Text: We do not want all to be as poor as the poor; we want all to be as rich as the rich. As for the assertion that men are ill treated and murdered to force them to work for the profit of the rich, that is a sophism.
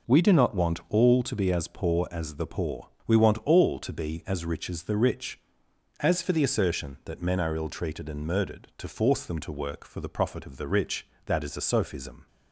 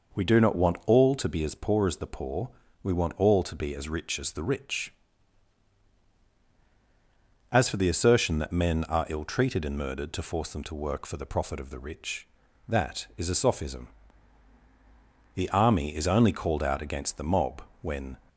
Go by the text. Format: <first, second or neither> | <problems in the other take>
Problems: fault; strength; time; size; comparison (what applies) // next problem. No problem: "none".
first | goes on to say "The army is only called out against the mob when"; strong; from 15.3 s on; 2.8 s long